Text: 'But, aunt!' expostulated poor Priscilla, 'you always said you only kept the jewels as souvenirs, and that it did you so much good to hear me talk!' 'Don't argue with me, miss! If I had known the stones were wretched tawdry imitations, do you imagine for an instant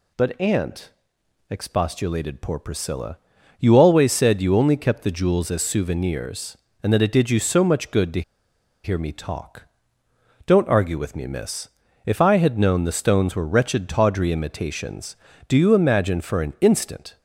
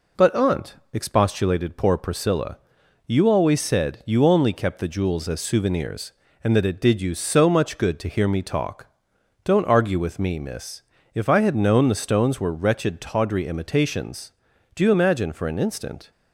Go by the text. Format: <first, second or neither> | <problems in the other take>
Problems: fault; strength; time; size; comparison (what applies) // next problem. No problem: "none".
second | pauses between "to" and "hear"; noticeable; at 8.2 s; 0.62 s long